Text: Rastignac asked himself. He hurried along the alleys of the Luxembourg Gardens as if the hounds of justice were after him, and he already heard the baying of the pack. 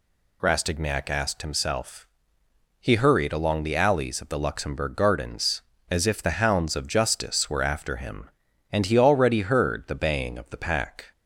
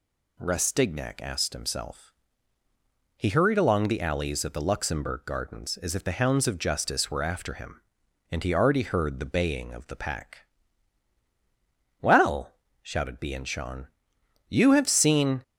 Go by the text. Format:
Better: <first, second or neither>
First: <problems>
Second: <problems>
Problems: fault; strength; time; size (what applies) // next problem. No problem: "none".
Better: first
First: none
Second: goes on to say "Well shouted Bianchon you have seen"; strong; from 12.0 s on; 3.4 s long